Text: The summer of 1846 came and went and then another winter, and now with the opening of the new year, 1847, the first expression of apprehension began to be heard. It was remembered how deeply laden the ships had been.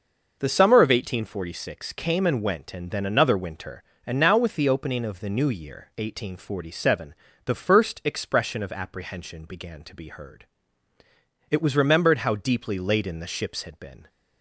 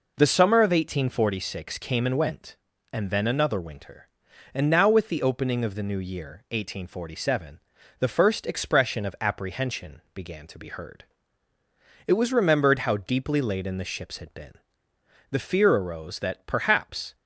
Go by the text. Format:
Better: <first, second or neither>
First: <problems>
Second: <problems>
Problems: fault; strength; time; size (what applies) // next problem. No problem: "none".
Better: first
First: none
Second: goes on to say "The fear arose that perhaps"; strong; from 15.3 s on; 1.8 s long